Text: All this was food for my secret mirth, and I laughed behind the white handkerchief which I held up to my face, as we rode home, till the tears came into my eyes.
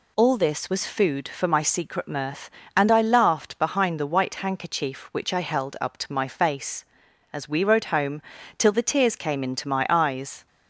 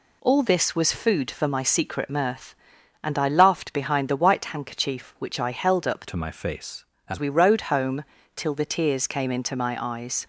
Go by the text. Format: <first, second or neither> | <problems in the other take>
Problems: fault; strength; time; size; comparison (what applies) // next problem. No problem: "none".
first | changes voice from "to" to "as"; from 6.0 to 7.1 s; 1.1 s long